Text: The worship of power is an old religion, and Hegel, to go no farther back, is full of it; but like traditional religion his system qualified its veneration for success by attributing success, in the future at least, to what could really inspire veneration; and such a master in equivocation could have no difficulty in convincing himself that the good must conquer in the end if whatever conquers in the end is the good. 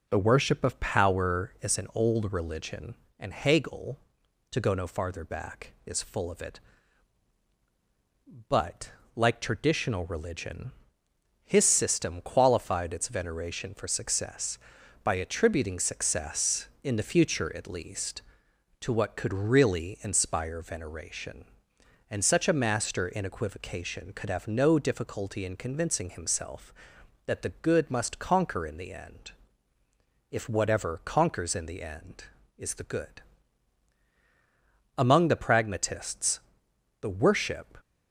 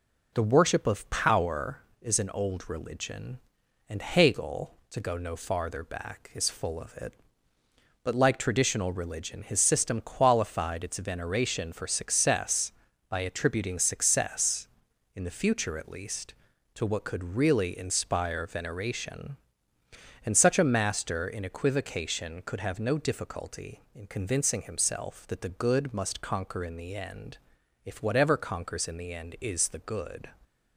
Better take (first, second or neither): second